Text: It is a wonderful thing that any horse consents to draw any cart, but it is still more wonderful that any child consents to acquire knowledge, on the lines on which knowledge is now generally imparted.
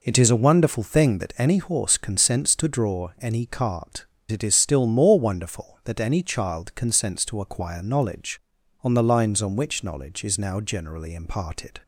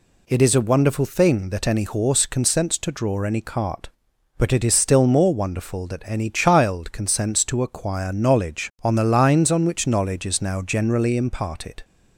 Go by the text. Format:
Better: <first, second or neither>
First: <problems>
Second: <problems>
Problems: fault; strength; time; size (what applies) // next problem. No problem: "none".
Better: second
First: skips "but"; at 4.1 s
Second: none